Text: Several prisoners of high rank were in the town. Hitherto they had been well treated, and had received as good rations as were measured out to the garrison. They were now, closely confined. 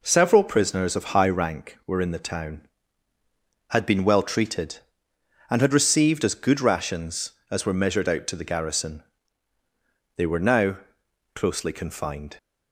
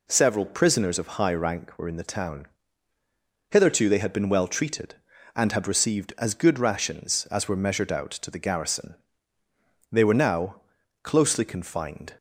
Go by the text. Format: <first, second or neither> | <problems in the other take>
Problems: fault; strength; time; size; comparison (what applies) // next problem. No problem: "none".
second | skips "Hitherto they"; at 3.1 s